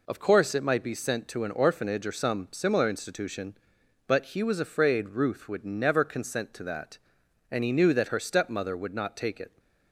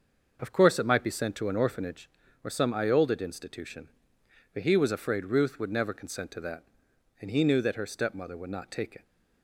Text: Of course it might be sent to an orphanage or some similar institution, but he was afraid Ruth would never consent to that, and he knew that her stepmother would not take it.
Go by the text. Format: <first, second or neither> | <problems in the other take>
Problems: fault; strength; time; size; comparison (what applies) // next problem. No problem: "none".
first | starts louder than the rest; noticeable; until 1.4 s; 6 dB // says "iolded" for "similar"; at 2.7 s